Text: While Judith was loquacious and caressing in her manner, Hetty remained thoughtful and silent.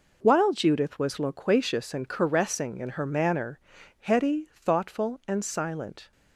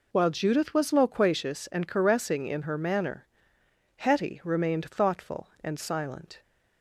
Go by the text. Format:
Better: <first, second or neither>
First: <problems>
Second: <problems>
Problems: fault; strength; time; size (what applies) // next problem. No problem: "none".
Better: second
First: skips "remained"; at 4.5 s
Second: none